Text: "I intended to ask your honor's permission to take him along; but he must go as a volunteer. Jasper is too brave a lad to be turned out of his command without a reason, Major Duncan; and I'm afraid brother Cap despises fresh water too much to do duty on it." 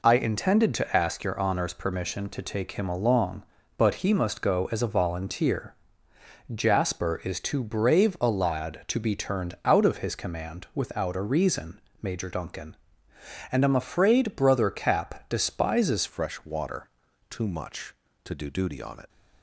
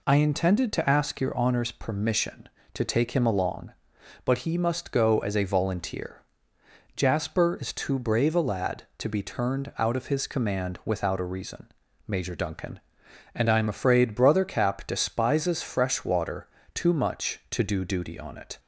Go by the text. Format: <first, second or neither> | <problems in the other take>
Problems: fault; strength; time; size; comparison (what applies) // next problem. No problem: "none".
second | changes voice at "fresh"; from 16.0 s on; 3.0 s long // pauses between "water" and "too"; at 16.8 s; 0.42 s long; slight in the second